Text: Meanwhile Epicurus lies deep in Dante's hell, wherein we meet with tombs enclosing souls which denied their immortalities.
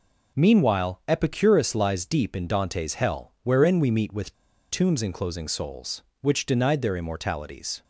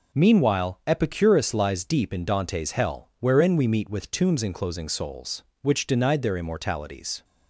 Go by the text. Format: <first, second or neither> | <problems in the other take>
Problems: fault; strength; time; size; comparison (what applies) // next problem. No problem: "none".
second | pauses between "with" and "tombs"; at 4.3 s; 0.36 s long